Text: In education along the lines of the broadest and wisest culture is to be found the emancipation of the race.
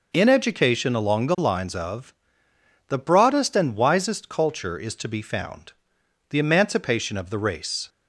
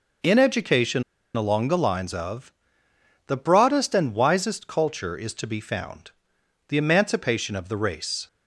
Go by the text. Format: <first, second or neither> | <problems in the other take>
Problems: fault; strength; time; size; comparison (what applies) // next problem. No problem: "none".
first | pauses between "education" and "along"; slight; at 1.0 s; 0.32 s long // pauses between "of" and "the"; noticeable; at 2.5 s; 0.72 s long; noticeable in the first // pauses between "found" and "the"; noticeable; at 6.1 s; 0.56 s long; noticeable in the first